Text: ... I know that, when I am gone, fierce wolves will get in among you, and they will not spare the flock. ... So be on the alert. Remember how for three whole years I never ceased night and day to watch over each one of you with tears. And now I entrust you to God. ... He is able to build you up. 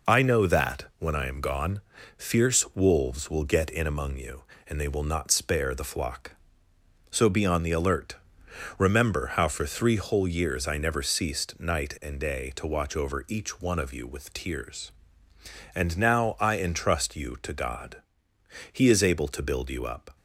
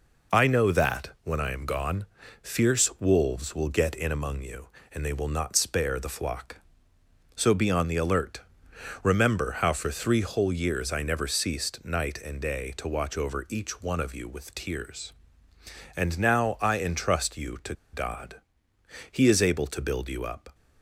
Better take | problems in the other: first | pauses between "to" and "God"; slight; at 17.7 s; 0.18 s long

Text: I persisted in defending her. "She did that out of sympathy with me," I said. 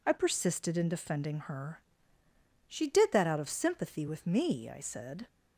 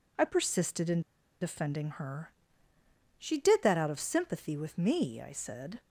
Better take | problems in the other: first | pauses between "in" and "defending"; at 1.0 s; 0.39 s long

